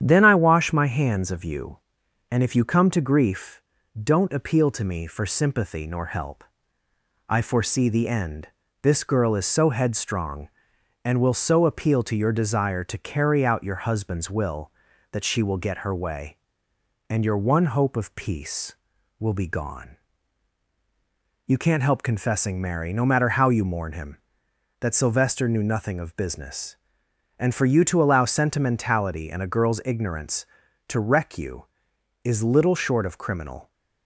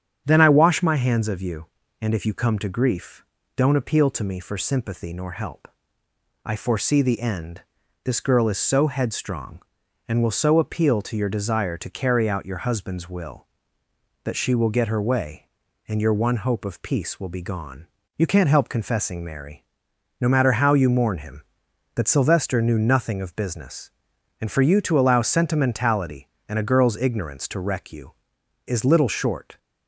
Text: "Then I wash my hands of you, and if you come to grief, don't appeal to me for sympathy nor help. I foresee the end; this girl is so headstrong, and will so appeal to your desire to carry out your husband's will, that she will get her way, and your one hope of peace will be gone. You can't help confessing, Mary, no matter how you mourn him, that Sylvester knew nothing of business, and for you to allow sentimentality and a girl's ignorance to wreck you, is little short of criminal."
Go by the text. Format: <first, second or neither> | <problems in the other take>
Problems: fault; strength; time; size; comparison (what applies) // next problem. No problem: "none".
first | starts louder than the rest; strong; until 1.2 s; 8 dB; strong in the first // stops before "of criminal"; at 29.5 s